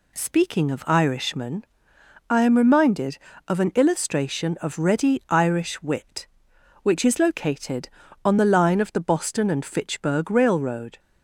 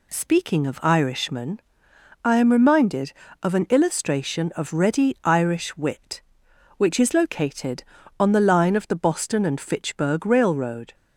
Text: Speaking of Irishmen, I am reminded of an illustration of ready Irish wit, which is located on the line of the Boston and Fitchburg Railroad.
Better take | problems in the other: neither | none

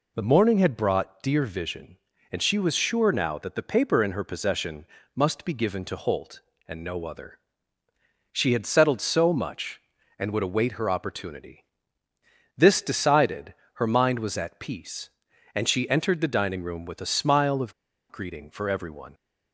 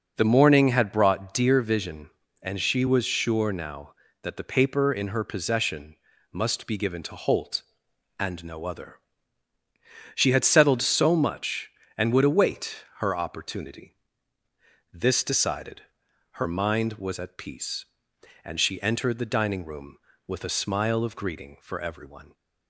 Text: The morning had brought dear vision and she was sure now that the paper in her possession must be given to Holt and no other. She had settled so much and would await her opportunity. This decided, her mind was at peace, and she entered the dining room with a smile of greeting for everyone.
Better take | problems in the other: second | pauses between "possession" and "must"; slight; at 4.8 s; 0.30 s long; slight in the second // pauses between "of" and "greeting"; at 17.7 s; 0.38 s long

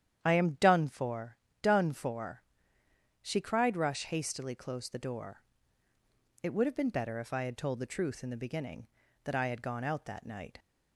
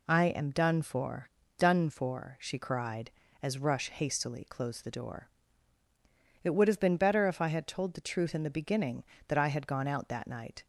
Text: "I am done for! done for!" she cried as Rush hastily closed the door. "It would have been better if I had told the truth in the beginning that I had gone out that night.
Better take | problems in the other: second | starts louder than the rest; strong; until 1.2 s; 9.5 dB // skips "as"; at 3.7 s

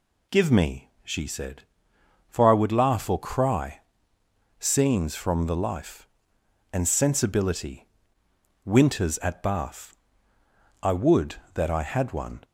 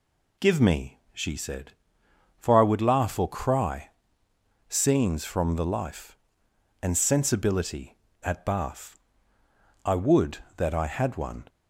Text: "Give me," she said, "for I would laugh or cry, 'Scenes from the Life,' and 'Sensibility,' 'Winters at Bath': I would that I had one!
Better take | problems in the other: first | skips "Winters"; at 8.0 s

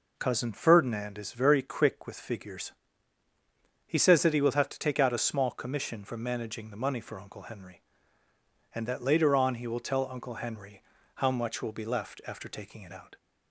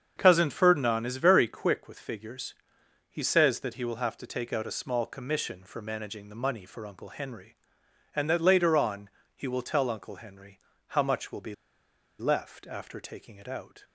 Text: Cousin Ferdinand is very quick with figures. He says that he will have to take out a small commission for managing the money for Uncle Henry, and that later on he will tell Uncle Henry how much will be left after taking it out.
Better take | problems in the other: first | starts louder than the rest; strong; until 1.1 s; 7.5 dB // pauses between "on" and "he"; slight; at 9.0 s; 0.26 s long // pauses between "Henry" and "how"; slight; at 10.5 s; 0.30 s long; slight in the first // pauses between "be" and "left"; noticeable; at 11.5 s; 0.65 s long

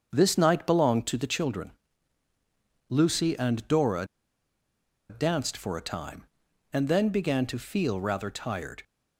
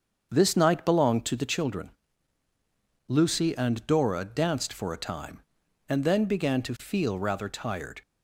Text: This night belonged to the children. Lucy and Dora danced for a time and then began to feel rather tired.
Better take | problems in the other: second | starts louder than the rest; strong; until 1.1 s; 7 dB; also in the second // pauses between "Dora" and "danced"; at 4.0 s; 1.0 s long

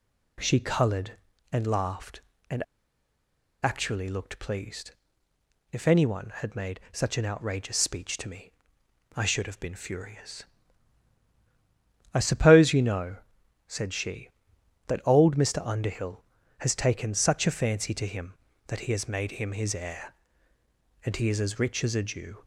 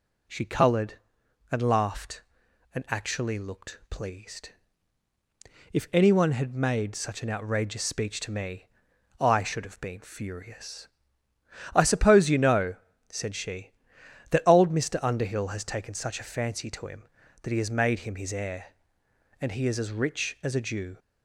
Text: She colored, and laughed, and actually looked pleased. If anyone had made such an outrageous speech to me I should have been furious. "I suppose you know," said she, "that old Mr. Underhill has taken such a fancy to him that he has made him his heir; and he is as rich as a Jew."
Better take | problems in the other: second | pauses between "and" and "actually"; at 2.6 s; 0.99 s long // pauses between "me" and "I"; noticeable; at 8.5 s; 0.64 s long; noticeable in the second

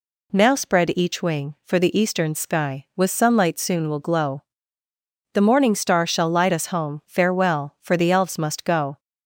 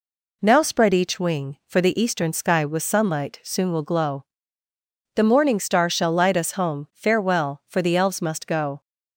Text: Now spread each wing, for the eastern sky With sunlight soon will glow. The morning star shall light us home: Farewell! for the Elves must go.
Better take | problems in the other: neither | none

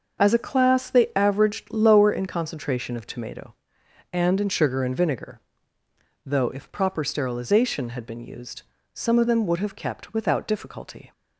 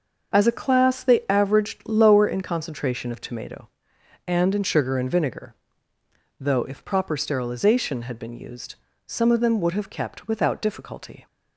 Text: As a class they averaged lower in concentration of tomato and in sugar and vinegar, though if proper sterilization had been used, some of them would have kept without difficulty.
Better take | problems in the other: neither | starts louder than the rest; the same in both

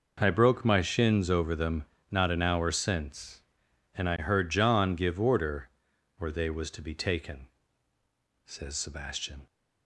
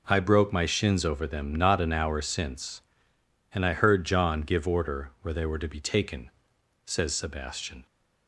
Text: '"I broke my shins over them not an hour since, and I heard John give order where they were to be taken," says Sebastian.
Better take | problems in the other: second | pauses between "them" and "not"; slight; at 1.8 s; 0.26 s long // pauses between "order" and "where"; noticeable; at 5.7 s; 0.48 s long // says "was" for "were"; at 6.5 s

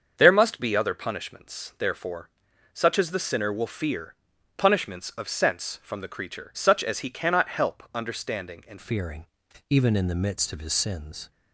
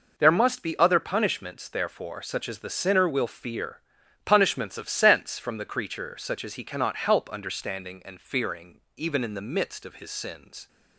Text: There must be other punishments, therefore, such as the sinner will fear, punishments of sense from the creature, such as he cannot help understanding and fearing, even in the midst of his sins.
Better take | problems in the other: second | starts louder than the rest; until 1.1 s; 7 dB // changes voice at "fearing"; from 8.7 s on; 2.6 s long

